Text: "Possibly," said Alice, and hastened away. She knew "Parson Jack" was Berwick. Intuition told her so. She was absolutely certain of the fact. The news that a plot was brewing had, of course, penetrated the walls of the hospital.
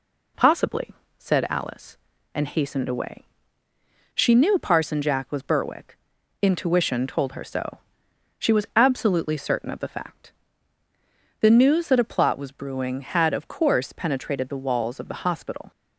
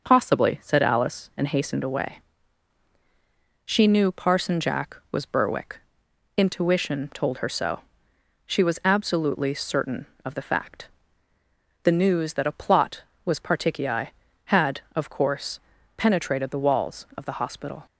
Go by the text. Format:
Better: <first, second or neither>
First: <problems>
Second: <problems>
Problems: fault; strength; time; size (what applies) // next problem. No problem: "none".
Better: first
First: none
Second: starts louder than the rest; noticeable; until 1.0 s; 6 dB // says "particii" for "brewing"; at 13.3 s